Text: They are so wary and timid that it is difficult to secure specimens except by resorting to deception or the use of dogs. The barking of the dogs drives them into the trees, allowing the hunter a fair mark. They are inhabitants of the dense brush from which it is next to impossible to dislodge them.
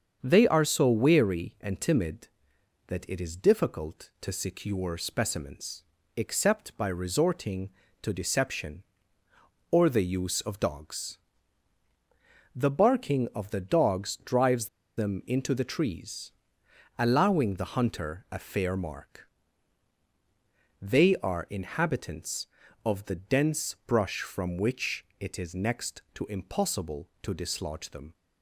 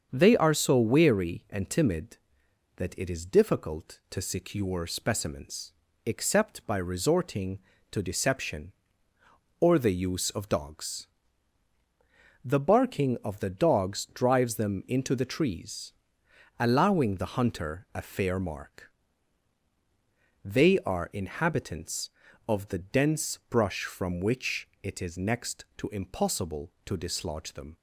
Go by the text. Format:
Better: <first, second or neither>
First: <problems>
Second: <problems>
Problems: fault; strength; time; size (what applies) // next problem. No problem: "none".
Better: second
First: starts louder than the rest; strong; until 1.2 s; 7 dB // pauses between "specimens" and "except"; slight; at 5.8 s; 0.32 s long // pauses between "drives" and "them"; slight; at 14.6 s; 0.30 s long // pauses between "which" and "it"; slight; at 25.0 s; 0.16 s long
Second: starts louder than the rest; until 1.1 s; 7 dB // pauses between "specimens" and "except"; slight; at 5.7 s; 0.32 s long // pauses between "which" and "it"; slight; at 24.6 s; 0.16 s long